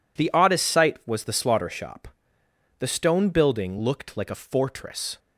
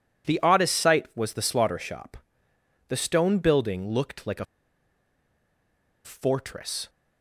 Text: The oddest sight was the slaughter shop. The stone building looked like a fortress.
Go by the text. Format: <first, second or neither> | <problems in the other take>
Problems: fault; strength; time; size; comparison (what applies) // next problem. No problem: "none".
first | pauses between "a" and "fortress"; strong; at 4.4 s; 1.5 s long